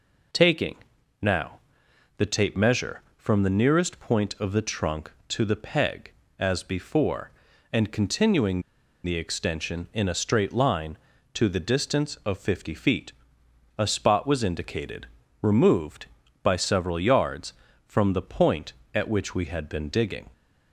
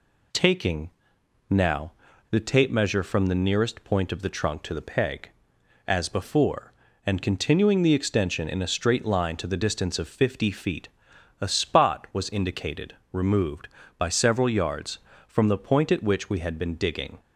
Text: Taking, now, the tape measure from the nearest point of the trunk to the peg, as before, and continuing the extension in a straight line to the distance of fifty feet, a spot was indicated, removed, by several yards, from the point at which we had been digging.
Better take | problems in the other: second | pauses between "continuing" and "the"; at 8.6 s; 0.43 s long

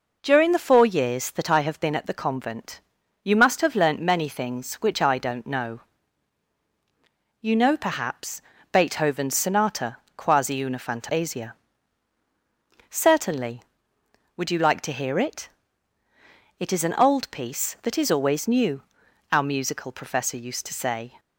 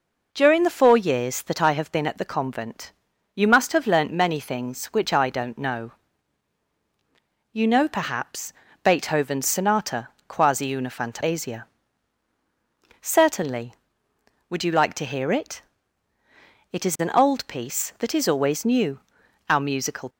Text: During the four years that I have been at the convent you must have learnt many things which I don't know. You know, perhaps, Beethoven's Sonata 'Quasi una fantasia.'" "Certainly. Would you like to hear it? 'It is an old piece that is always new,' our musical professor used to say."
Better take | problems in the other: first | pauses between "convent" and "you"; at 2.9 s; 0.42 s long; also in the first // pauses between "Sonata" and "Quasi"; slight; at 10.0 s; 0.18 s long; slight in the first // stops before "professor used to say"; at 20.0 s

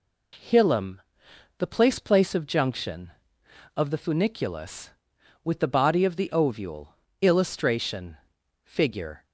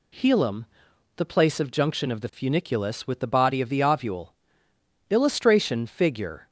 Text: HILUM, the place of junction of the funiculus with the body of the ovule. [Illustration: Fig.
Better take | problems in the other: second | says "place" twice; at 1.9 s

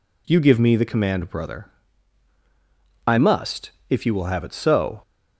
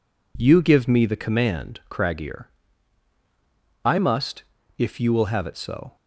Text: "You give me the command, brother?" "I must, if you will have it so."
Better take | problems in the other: first | says "craggier" for "brother"; at 1.9 s

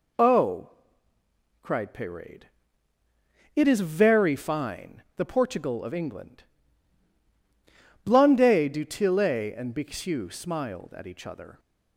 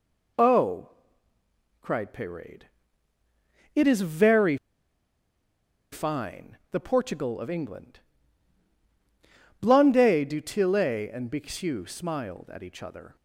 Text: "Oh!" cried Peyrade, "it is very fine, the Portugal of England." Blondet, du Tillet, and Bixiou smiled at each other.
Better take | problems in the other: first | pauses between "very" and "fine"; strong; at 4.5 s; 1.3 s long

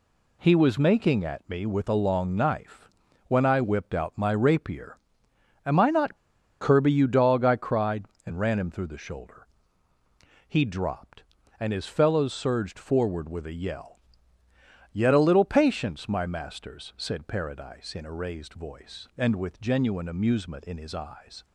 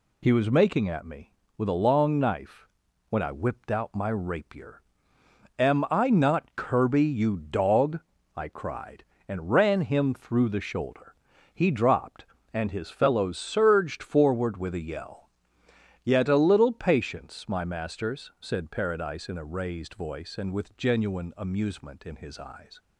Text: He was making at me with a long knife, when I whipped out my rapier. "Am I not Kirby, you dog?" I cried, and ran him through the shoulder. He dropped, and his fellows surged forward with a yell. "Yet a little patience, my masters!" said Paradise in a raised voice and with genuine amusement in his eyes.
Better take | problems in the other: second | pauses between "not" and "Kirby"; at 6.1 s; 0.43 s long

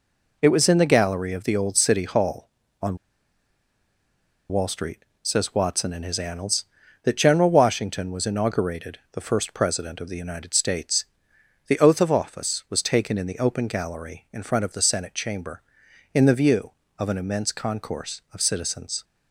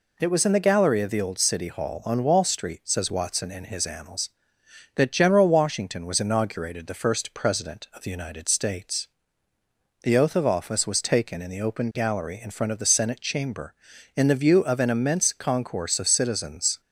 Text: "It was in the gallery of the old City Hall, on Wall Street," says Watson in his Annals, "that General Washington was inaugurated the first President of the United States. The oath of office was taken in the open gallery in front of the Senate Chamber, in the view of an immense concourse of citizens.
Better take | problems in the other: second | pauses between "on" and "Wall"; strong; at 2.9 s; 1.5 s long

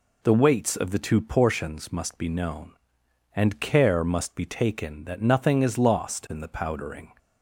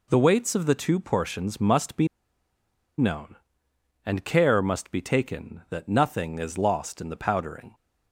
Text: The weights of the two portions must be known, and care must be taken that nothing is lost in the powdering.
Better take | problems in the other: first | pauses between "be" and "known"; noticeable; at 2.0 s; 0.91 s long

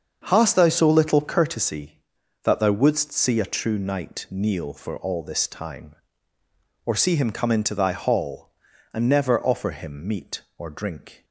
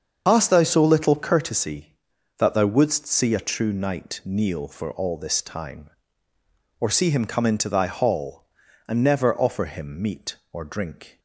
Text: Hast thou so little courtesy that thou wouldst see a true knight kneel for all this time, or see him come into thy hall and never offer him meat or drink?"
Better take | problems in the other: first | loses the start of "Hast"; at 0.2 s; 90 ms // starts louder than the rest; until 1.2 s; 7 dB; also in the first

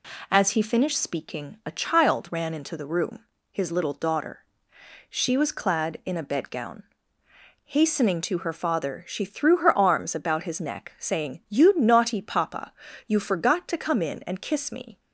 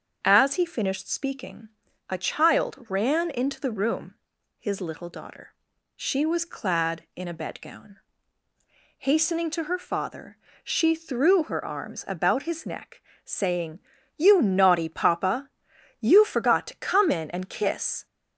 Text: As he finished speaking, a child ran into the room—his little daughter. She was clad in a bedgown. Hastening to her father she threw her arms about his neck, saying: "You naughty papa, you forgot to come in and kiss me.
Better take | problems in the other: first | starts louder than the rest; until 1.2 s; 7 dB // pauses between "father" and "she"; slight; at 10.3 s; 0.26 s long // stops before "me"; at 18.0 s

